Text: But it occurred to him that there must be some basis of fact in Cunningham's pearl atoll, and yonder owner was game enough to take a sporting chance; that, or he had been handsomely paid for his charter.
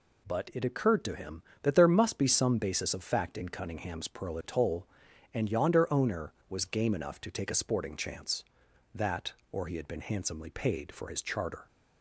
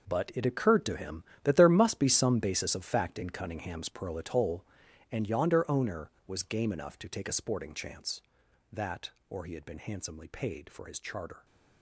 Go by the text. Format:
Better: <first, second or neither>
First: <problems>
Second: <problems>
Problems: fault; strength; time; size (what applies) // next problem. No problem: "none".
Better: first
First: none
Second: gets quieter; strong; throughout; 12.5 dB